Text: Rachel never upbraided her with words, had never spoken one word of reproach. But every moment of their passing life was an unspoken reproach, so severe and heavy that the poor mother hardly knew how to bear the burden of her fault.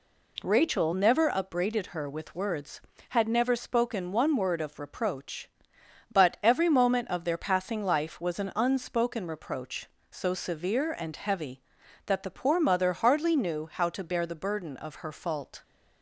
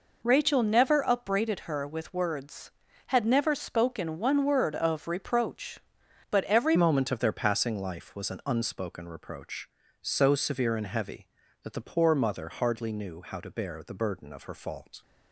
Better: first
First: none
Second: changes voice at "moment"; from 6.7 s on; 8.3 s long

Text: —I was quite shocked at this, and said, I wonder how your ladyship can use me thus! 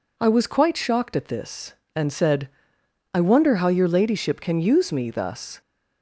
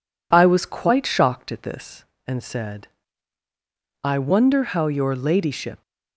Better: first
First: none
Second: stops before "can use me thus"; at 5.8 s

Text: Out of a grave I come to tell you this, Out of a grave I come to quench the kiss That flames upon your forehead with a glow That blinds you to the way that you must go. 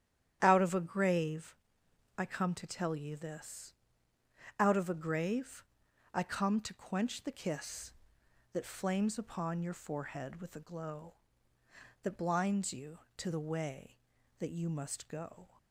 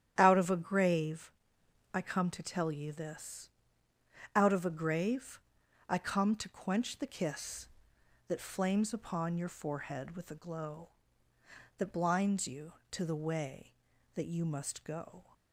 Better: neither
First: starts louder than the rest; strong; until 1.4 s; 10.5 dB // pauses between "grave" and "I"; noticeable; at 1.5 s; 0.62 s long // pauses between "grave" and "I"; noticeable; at 5.6 s; 0.50 s long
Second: starts louder than the rest; strong; until 1.1 s; 10.5 dB // pauses between "grave" and "I"; noticeable; at 1.2 s; 0.62 s long // pauses between "grave" and "I"; noticeable; at 5.3 s; 0.49 s long

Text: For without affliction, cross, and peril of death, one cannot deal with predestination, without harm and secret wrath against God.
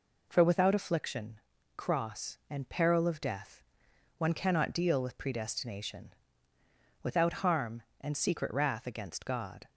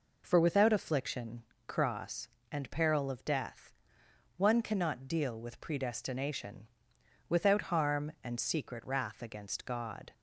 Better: neither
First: none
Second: none

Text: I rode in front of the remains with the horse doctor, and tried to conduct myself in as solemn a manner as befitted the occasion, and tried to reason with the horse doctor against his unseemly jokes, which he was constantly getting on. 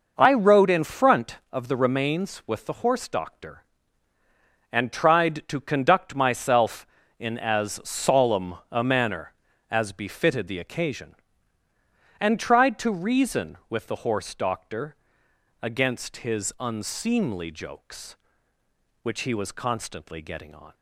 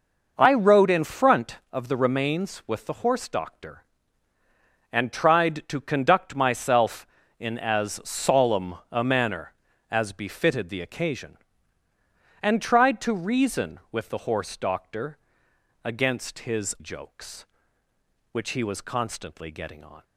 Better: first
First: pauses between "solemn" and "a"; slight; at 8.5 s; 0.16 s long // pauses between "doctor" and "against"; noticeable; at 14.9 s; 0.70 s long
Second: pauses between "solemn" and "a"; slight; at 8.7 s; 0.16 s long // pauses between "doctor" and "against"; noticeable; at 15.1 s; 0.70 s long // skips "unseemly"; at 16.7 s

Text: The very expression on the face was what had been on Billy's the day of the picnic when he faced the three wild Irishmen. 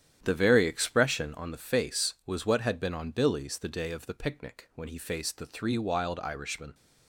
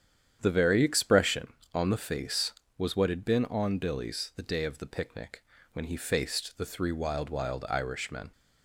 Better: first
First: starts louder than the rest; strong; until 1.2 s; 10 dB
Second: starts louder than the rest; strong; until 1.4 s; 9 dB // pauses between "picnic" and "when"; slight; at 5.4 s; 0.30 s long // says "wild" twice; at 7.2 s

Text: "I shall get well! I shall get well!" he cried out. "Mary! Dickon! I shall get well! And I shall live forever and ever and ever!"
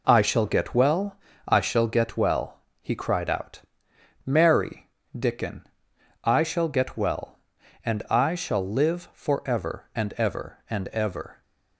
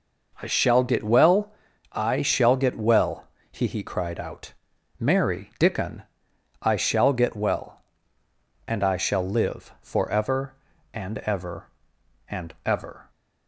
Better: first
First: none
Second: says "he" twice; at 3.6 s

